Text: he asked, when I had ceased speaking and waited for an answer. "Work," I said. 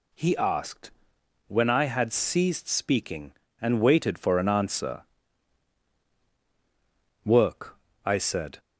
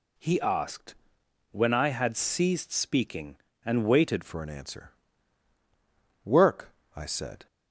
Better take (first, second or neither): first